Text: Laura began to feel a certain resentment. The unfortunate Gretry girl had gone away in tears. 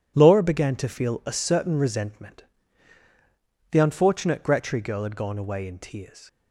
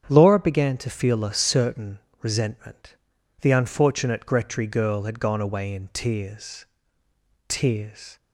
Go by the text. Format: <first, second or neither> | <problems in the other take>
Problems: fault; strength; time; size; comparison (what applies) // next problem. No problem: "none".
first | starts louder than the rest; strong; until 1.1 s; 8 dB // pauses between "certain" and "resentment"; slight; at 1.9 s; 0.22 s long // says "tears" twice; at 7.4 s